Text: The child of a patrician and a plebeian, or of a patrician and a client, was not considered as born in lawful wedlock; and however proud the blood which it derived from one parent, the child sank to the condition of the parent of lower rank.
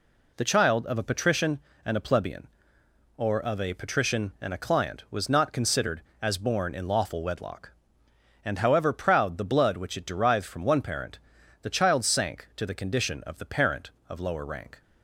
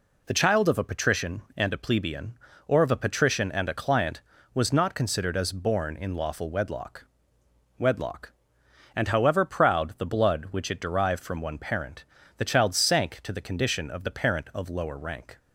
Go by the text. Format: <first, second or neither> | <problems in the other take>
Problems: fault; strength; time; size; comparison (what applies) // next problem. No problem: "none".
first | says "wedlock" twice; at 7.7 s